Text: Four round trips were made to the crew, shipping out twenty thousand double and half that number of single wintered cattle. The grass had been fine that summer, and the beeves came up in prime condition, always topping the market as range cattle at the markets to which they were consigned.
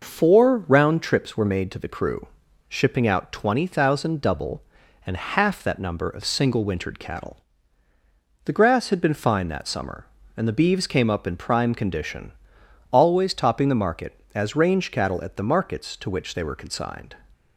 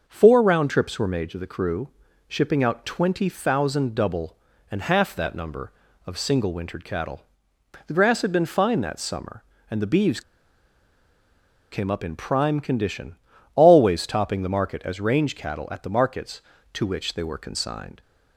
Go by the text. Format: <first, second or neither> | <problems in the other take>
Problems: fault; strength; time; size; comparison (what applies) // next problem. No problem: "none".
first | starts louder than the rest; until 1.0 s; 6 dB // pauses between "beeves" and "came"; strong; at 10.2 s; 1.5 s long